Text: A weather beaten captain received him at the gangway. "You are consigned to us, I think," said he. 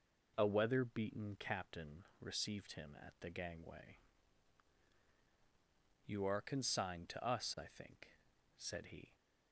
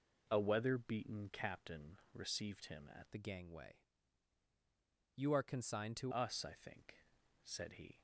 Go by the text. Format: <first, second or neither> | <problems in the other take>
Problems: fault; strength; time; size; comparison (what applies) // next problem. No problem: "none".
first | changes voice from "the" to "to"; from 3.1 to 6.1 s; 3.0 s long